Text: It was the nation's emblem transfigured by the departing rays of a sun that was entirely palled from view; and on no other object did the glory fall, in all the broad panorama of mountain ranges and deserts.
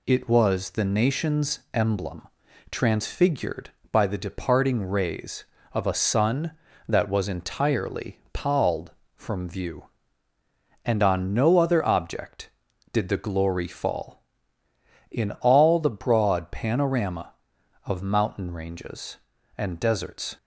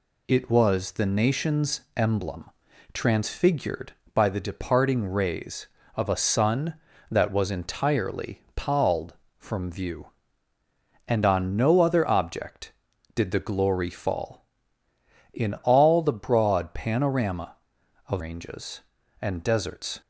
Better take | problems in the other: first | pauses between "nation's" and "emblem"; slight; at 1.8 s; 0.16 s long // pauses between "emblem" and "transfigured"; at 2.4 s; 0.44 s long; also in the first // skips "mountain"; at 18.2 s

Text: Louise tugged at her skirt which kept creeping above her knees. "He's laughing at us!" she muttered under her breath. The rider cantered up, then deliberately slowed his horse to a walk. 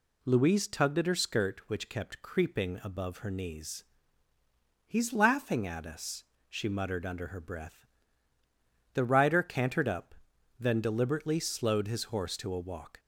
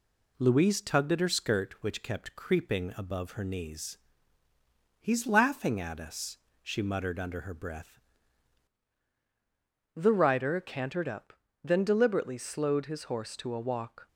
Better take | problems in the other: first | changes voice at "The"; from 9.9 s on; 4.1 s long

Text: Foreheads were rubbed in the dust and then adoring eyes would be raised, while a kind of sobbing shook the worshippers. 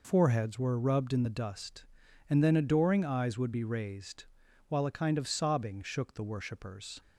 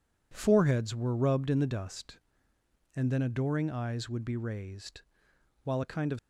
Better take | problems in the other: first | stops before "sobbing shook the worshippers"; at 6.1 s

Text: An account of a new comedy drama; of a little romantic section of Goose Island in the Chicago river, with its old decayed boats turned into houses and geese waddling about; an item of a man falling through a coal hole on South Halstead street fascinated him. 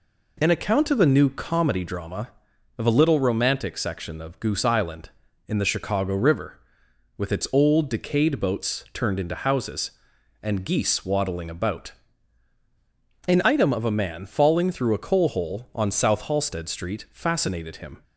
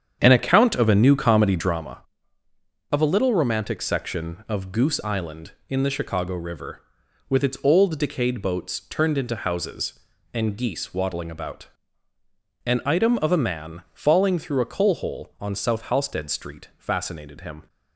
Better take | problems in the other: first | starts louder than the rest; strong; until 2.0 s; 8 dB

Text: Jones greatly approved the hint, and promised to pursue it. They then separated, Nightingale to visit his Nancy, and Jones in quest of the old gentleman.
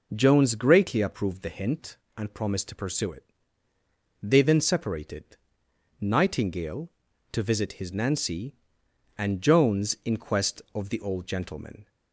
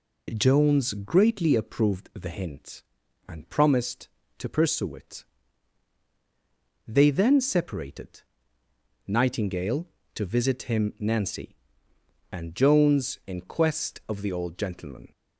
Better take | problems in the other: first | says "him" for "his"; at 10.6 s

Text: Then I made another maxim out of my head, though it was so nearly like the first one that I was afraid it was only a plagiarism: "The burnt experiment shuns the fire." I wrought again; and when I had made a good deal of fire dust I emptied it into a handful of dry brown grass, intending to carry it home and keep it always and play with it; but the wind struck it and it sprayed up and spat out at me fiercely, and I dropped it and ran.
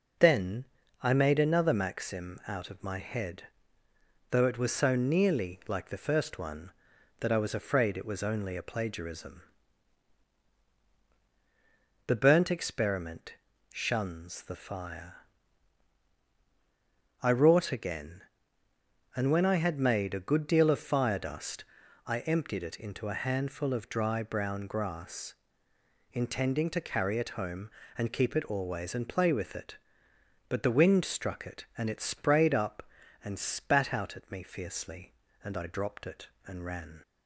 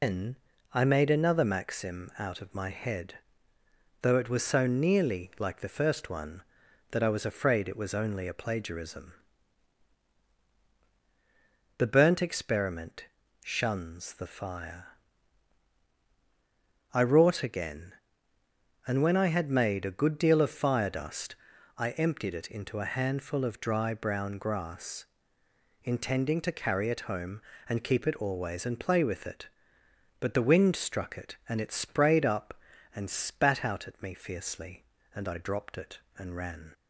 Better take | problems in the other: first | loses the start of "Then"; at 0.0 s; 115 ms // pauses between "Then" and "I"; at 0.3 s; 0.38 s long; also in the first // pauses between "experiment" and "shuns"; at 13.0 s; 0.40 s long; also in the first // pauses between "dust" and "I"; at 21.3 s; 0.40 s long; also in the first

